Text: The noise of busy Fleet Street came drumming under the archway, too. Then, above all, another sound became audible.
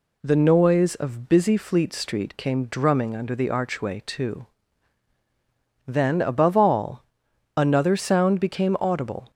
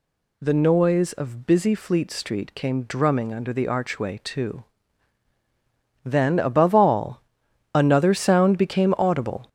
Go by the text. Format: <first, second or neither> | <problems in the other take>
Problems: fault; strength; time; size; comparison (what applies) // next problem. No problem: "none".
first | gets louder; throughout; 6.5 dB